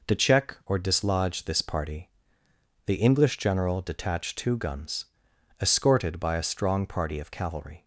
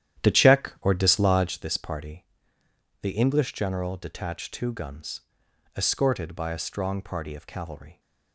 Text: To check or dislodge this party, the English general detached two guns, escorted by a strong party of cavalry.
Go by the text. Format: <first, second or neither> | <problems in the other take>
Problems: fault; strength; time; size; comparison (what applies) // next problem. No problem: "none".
first | starts louder than the rest; strong; until 1.6 s; 11 dB